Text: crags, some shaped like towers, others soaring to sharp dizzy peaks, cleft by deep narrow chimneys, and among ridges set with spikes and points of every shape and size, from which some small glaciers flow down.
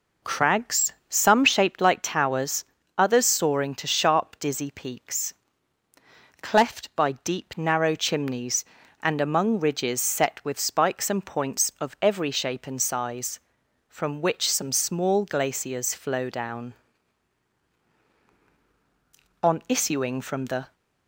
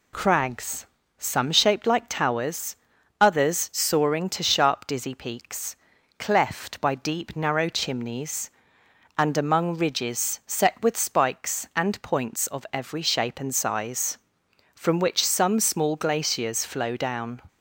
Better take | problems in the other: second | goes on to say "On issuing from the"; from 19.4 s on; 1.3 s long

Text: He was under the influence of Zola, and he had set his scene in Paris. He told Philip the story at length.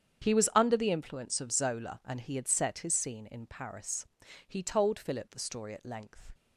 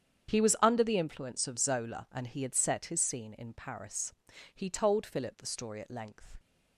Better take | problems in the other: neither | starts louder than the rest; strong; the same in both

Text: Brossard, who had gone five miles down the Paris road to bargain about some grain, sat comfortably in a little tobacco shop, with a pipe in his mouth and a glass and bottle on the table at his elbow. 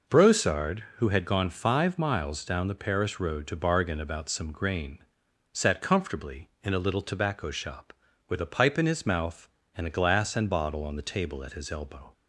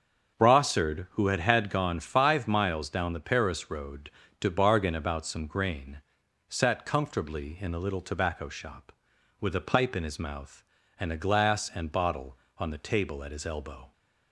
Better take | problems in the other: first | starts louder than the rest; until 1.4 s; 7 dB // says "had" twice; at 1.3 s

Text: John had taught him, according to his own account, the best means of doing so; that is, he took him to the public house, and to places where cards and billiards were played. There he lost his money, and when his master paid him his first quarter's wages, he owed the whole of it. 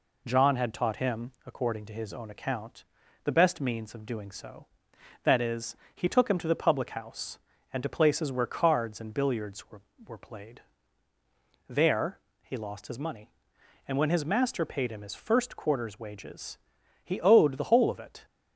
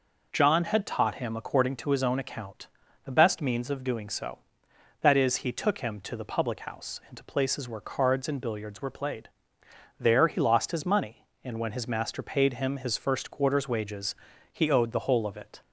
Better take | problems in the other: second | says "were" twice; at 10.0 s // pauses between "There" and "he"; slight; at 12.1 s; 0.22 s long

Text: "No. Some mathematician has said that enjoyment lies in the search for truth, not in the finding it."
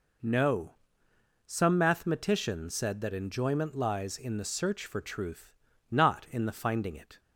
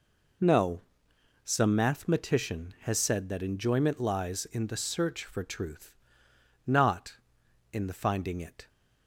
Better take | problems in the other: second | skips "has"; at 2.7 s

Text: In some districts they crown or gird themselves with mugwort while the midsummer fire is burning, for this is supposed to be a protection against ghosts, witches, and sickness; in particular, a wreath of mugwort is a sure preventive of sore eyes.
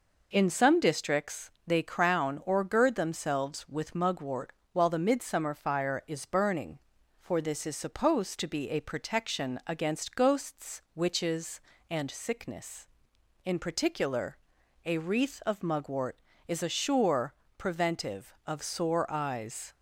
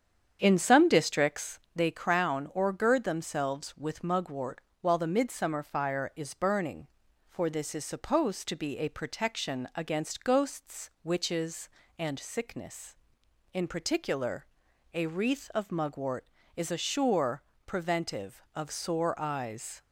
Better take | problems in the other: first | starts louder than the rest; strong; until 1.8 s; 8 dB // pauses between "districts" and "they"; slight; at 1.5 s; 0.18 s long; slight in the first // pauses between "mugwort" and "while"; slight; at 4.6 s; 0.18 s long; slight in the first // pauses between "sure" and "preventive"; slight; at 17.4 s; 0.24 s long; slight in the first

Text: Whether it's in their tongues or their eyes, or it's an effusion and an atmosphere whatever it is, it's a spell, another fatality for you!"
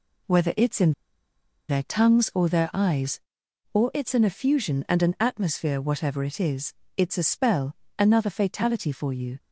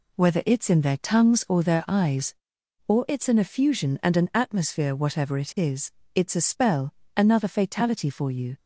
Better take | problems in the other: second | pauses between "in" and "their"; noticeable; at 0.9 s; 0.76 s long

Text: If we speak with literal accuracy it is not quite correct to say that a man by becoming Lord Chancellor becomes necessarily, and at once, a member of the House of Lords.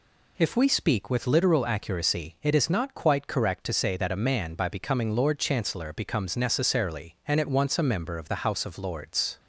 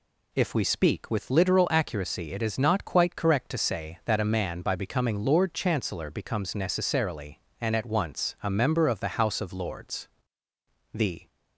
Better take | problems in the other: first | goes on to say "The"; slight; from 10.9 s on; 0.34 s long

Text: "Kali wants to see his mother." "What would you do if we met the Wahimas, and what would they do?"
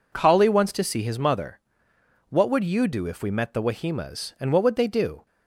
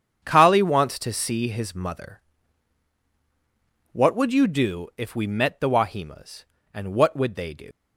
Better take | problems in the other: first | starts louder than the rest; strong; until 1.2 s; 7.5 dB // leaves "do" unfinished; at 7.7 s; 90 ms

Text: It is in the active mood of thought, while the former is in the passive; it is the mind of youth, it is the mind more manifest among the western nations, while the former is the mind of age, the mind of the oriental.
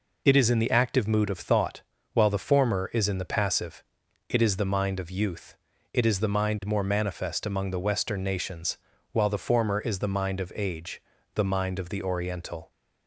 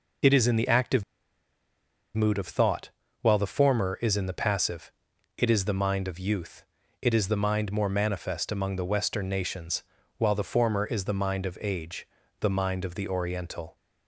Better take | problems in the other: first | pauses between "active" and "mood"; at 1.0 s; 1.1 s long

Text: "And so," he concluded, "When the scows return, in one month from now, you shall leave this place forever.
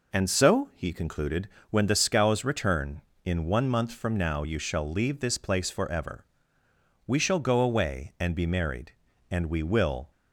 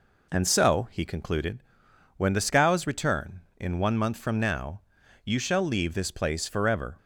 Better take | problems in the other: second | goes on to say "We shall go away and be married and we will"; strong; from 7.0 s on; 3.0 s long

